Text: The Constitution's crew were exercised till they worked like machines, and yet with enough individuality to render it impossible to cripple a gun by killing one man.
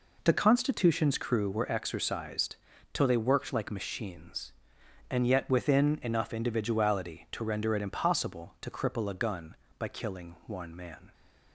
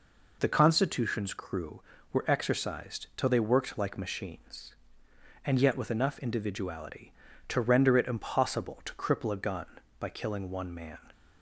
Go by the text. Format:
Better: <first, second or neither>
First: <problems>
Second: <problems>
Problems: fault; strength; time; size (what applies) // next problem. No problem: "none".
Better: second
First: pauses between "exercised" and "till"; slight; at 2.5 s; 0.36 s long // says "within" for "with"; at 5.4 s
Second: none